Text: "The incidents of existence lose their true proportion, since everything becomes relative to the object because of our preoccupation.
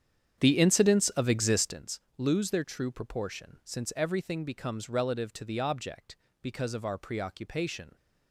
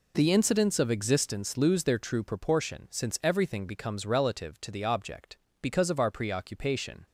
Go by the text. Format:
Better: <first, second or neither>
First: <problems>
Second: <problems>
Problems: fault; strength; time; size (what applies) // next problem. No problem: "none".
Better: second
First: starts louder than the rest; strong; until 1.8 s; 8.5 dB // pauses between "existence" and "lose"; slight; at 2.0 s; 0.16 s long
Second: none